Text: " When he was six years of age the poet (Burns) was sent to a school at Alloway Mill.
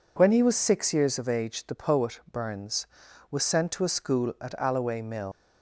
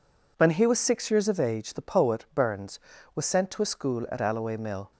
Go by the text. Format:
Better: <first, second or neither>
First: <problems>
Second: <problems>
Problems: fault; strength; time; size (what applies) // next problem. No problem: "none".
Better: second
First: leaves "Mill" unfinished; at 5.3 s; 115 ms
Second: none